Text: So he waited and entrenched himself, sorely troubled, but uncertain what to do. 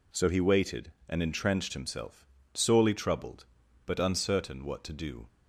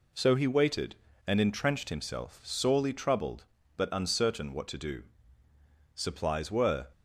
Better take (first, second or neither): first